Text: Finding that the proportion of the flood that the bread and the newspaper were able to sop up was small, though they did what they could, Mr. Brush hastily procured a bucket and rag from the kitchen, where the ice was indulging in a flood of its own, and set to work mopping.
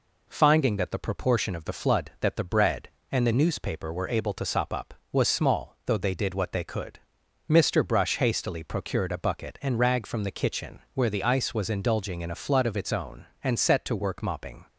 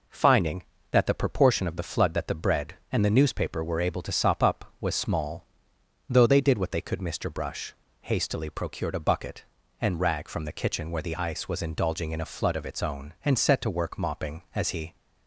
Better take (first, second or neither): first